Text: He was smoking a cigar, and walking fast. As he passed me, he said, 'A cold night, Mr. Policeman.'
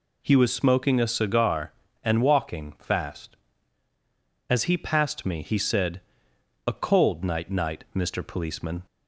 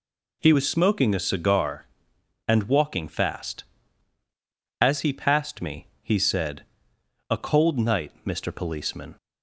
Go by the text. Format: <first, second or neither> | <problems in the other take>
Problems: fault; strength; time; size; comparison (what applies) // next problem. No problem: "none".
second | says "night" twice; at 7.4 s